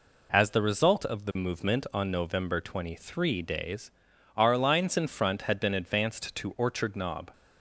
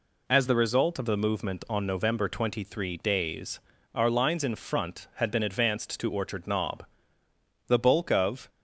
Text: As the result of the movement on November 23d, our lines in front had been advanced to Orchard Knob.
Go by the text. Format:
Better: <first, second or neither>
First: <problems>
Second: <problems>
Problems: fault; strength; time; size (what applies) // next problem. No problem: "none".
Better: first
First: none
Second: goes on to say "The bulk of"; noticeable; from 7.6 s on; 0.82 s long